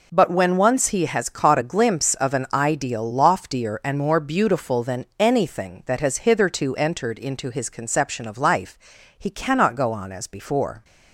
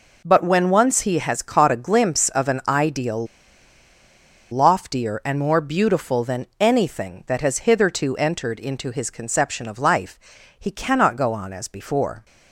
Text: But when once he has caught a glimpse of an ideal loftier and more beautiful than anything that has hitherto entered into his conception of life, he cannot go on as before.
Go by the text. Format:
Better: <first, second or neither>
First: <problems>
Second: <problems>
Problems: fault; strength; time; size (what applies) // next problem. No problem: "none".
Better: first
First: none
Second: pauses between "ideal" and "loftier"; strong; at 3.2 s; 1.2 s long